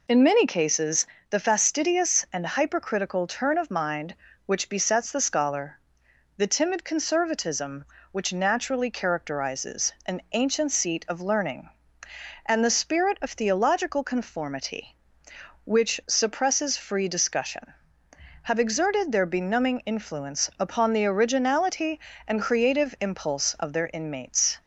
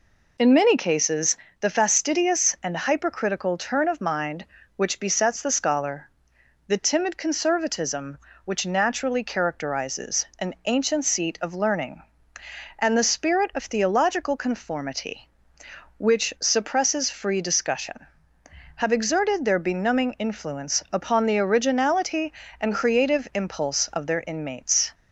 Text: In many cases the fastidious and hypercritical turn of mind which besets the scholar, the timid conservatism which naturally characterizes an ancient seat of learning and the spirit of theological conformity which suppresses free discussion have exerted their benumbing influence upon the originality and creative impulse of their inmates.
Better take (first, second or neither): neither